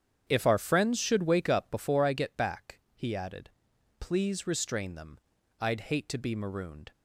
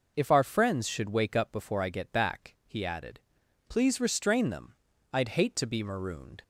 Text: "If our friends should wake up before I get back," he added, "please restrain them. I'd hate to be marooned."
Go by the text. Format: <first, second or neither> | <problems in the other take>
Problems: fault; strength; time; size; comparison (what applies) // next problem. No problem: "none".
second | starts louder than the rest; strong; until 1.9 s; 8.5 dB